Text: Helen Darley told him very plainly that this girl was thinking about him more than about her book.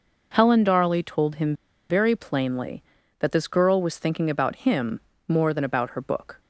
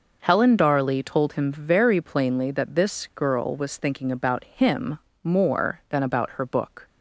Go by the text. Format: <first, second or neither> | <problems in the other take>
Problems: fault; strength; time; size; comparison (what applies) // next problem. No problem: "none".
second | pauses between "him" and "very"; slight; at 1.5 s; 0.35 s long // pauses between "him" and "more"; slight; at 4.9 s; 0.30 s long; slight in the second